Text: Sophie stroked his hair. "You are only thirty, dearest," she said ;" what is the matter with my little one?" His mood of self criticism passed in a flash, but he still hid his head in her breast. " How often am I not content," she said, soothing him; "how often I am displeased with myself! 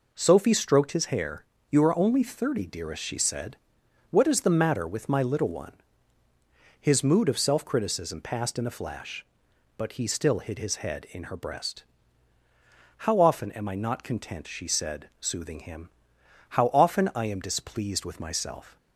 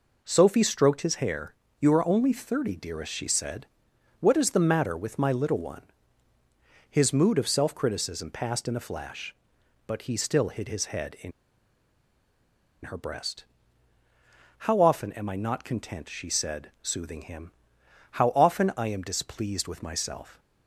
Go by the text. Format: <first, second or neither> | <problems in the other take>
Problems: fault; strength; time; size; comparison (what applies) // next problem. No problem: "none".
first | pauses between "in" and "her"; strong; at 11.3 s; 1.5 s long